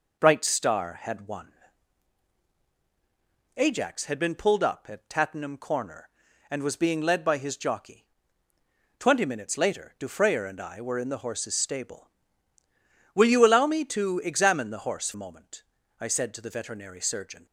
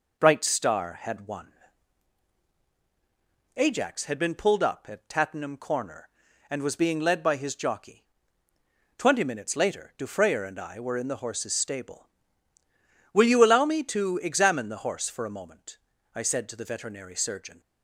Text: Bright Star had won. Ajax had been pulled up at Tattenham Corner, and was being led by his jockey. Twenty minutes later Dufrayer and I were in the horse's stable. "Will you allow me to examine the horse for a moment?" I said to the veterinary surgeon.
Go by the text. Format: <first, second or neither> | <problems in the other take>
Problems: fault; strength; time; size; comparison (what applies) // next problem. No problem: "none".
second | skips "for"; at 15.1 s